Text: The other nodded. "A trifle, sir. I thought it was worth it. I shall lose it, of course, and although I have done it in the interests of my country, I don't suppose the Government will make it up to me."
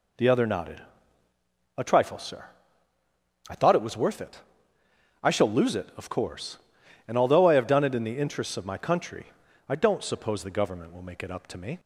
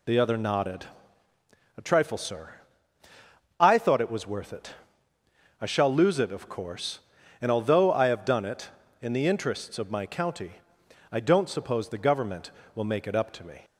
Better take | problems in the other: first | says "county" for "country"; at 10.0 s

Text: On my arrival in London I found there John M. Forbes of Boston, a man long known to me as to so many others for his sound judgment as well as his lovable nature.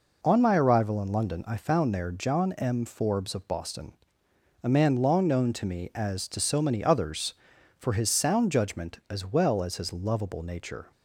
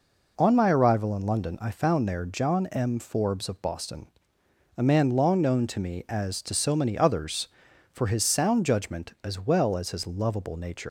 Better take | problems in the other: first | leaves "nature" unfinished; at 10.8 s; 160 ms

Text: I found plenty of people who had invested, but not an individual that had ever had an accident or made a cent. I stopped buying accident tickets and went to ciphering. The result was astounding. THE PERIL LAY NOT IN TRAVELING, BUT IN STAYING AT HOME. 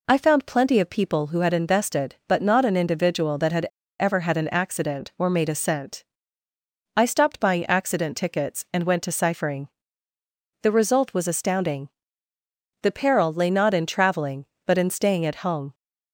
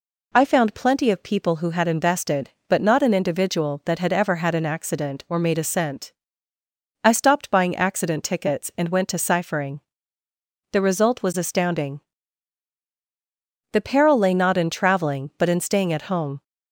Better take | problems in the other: second | pauses between "had" and "ever"; slight; at 3.6 s; 0.35 s long

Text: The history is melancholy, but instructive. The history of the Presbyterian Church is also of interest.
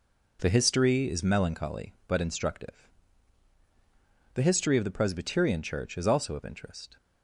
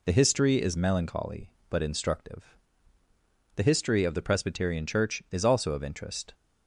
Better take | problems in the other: neither | none

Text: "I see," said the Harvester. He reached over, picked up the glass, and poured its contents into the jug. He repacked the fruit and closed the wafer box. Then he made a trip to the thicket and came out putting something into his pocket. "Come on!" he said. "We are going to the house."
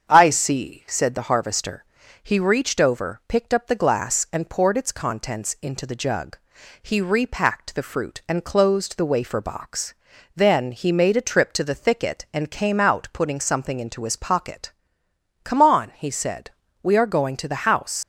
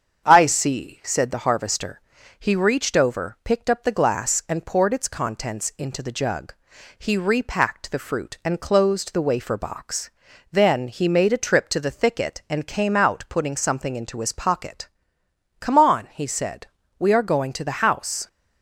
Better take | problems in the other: second | starts louder than the rest; strong; until 1.1 s; 7.5 dB; strong in the second // leaves "house" unfinished; at 18.0 s; 80 ms

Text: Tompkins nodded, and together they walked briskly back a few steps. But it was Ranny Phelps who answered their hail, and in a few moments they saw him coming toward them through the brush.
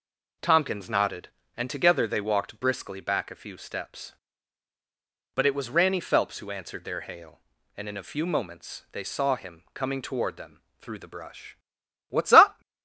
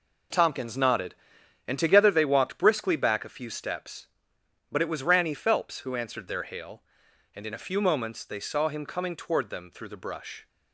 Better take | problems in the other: second | pauses between "them" and "through"; slight; at 10.6 s; 0.16 s long // goes on to say "What's up"; from 12.0 s on; 0.52 s long

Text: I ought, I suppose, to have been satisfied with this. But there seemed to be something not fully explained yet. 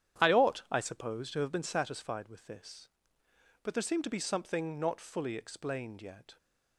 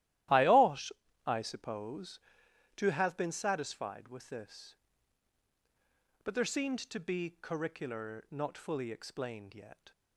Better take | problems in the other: first | starts louder than the rest; strong; until 1.6 s; 14 dB; strong in the first // says "curricular" for "something"; at 7.4 s

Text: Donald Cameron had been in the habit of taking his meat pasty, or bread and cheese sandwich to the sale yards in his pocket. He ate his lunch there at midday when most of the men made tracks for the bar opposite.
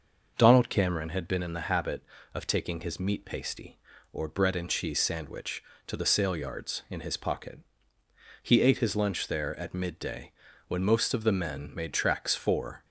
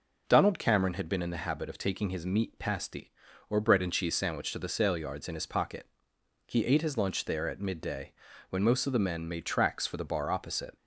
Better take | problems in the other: second | pauses between "midday" and "when"; slight; at 10.3 s; 0.34 s long; slight in the second // stops before "the bar opposite"; at 12.8 s

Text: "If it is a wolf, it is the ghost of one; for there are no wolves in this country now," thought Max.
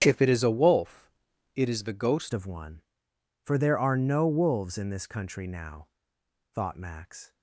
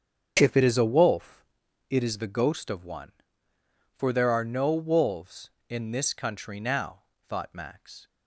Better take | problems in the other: second | starts louder than the rest; strong; until 1.0 s; 9 dB; strong in the second // changes voice at "of"; from 2.3 s on; 5.0 s long

